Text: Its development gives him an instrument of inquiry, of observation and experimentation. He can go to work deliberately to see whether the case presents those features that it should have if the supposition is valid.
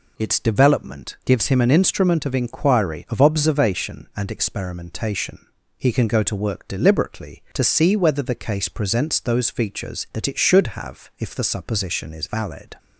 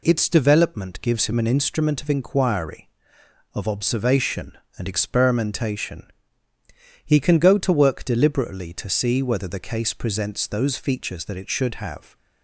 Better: first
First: none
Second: stops before "if the supposition is valid"; at 12.1 s

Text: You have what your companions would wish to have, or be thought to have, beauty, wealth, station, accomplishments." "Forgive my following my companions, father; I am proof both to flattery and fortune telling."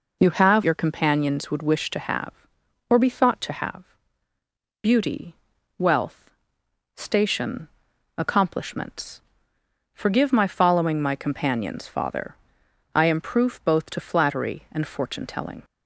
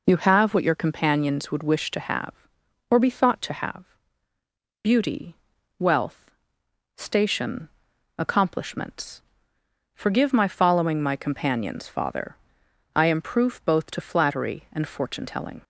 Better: second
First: skips "what"; at 0.6 s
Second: none

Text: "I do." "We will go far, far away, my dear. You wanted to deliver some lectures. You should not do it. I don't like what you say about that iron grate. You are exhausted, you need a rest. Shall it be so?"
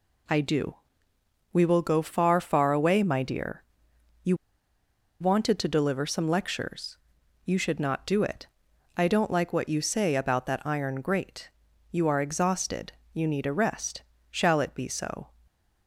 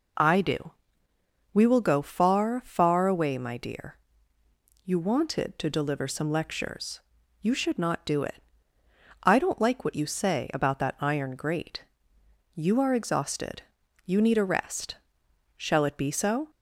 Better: second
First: pauses between "You" and "wanted"; noticeable; at 4.3 s; 0.84 s long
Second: none

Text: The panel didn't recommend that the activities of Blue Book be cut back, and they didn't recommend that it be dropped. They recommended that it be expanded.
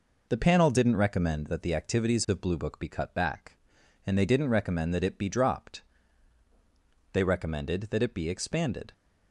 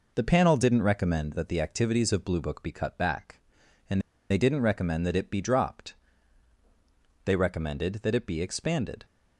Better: first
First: none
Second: pauses between "and" and "they"; slight; at 4.0 s; 0.29 s long

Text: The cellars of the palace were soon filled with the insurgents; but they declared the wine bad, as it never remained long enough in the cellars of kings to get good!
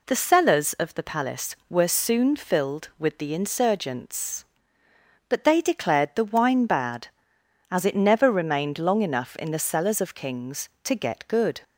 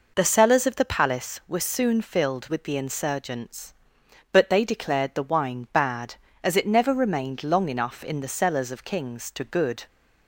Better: first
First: none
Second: skips "get"; at 9.4 s

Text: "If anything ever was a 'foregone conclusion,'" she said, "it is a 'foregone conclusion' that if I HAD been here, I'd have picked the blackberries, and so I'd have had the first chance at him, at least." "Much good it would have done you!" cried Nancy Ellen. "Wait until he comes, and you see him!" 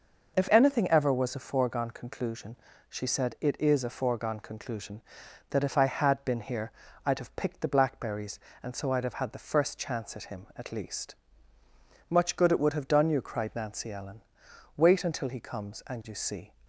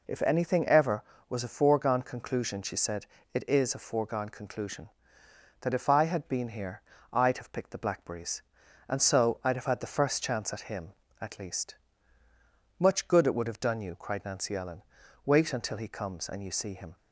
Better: second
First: stops before "him"; at 16.6 s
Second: none

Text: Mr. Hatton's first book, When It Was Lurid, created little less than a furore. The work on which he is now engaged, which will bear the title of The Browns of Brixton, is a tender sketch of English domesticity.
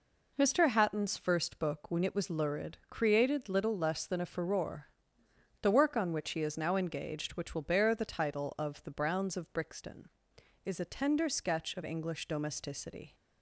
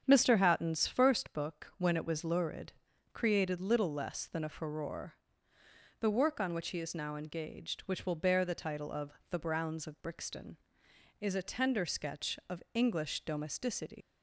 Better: first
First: none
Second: starts louder than the rest; strong; until 1.0 s; 7.5 dB // pauses between "of" and "The"; slight; at 9.1 s; 0.18 s long // leaves "domesticity" unfinished; at 14.0 s; 75 ms

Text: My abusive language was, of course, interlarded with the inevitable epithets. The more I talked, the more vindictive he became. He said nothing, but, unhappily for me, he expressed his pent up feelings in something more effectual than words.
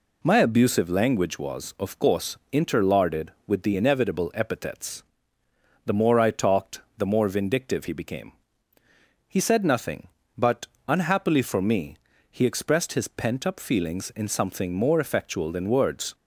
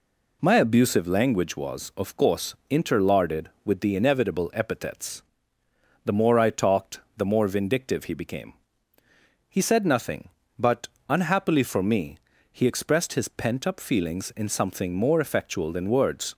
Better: neither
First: none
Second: none

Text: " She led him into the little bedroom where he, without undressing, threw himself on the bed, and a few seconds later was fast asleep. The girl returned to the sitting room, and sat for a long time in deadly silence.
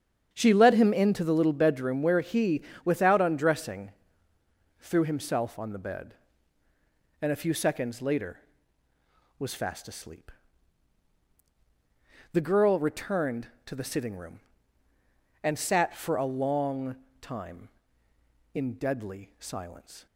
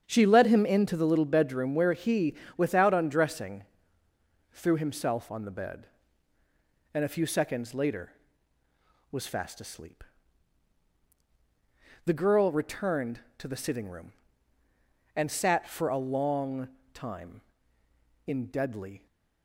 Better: first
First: starts louder than the rest; strong; until 1.3 s; 8 dB // pauses between "long" and "time"; slight; at 16.9 s; 0.24 s long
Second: starts louder than the rest; strong; until 1.0 s; 8 dB // pauses between "long" and "time"; slight; at 16.6 s; 0.24 s long // stops before "silence"; at 19.0 s

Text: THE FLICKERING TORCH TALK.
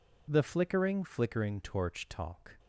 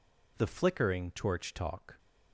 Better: second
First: says "FLICKERING" twice; at 1.0 s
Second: none

